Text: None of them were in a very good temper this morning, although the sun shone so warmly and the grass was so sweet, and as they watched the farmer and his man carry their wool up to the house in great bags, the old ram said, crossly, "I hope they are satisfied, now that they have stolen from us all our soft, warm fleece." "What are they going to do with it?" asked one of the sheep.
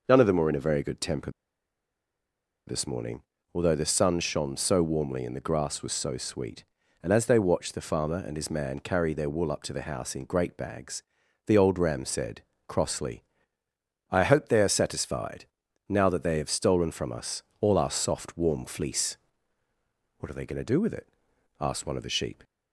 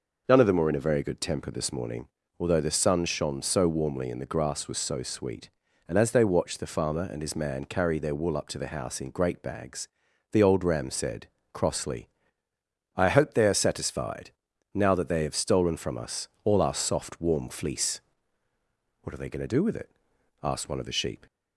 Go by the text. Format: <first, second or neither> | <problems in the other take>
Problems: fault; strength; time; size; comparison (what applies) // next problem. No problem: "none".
second | pauses between "temper" and "this"; strong; at 1.3 s; 1.3 s long // pauses between "us" and "all"; slight; at 17.4 s; 0.20 s long; slight in the second